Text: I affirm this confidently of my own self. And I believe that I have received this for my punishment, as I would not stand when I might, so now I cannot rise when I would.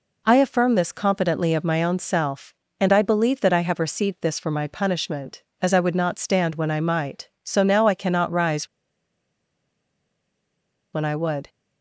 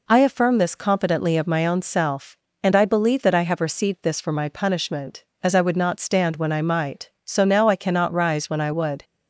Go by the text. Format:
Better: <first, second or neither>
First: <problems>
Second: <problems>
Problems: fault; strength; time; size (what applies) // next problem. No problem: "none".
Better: second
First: pauses between "rise" and "when"; strong; at 8.6 s; 2.2 s long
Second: none